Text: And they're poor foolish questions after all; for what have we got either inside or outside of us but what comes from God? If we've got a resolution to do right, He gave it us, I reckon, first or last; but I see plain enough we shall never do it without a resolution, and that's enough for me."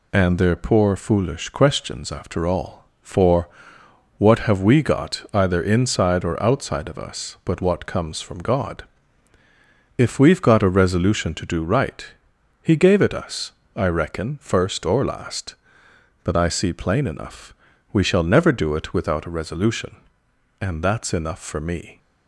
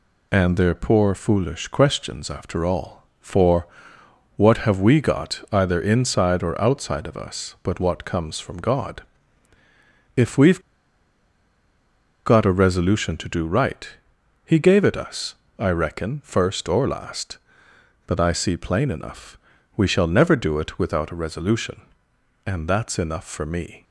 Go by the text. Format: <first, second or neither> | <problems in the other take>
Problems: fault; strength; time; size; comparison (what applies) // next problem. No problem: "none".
first | pauses between "for" and "what"; noticeable; at 3.6 s; 0.68 s long; noticeable in the first // pauses between "we've" and "got"; strong; at 10.5 s; 1.6 s long // pauses between "enough" and "we"; at 19.3 s; 0.38 s long; also in the first